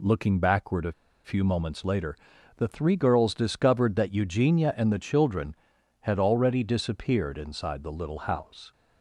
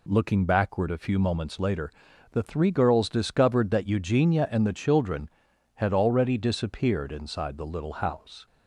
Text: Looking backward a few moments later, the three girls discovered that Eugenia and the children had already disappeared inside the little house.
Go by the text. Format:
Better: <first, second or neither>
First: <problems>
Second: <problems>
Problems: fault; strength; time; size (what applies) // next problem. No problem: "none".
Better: second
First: pauses between "a" and "few"; slight; at 0.9 s; 0.33 s long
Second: none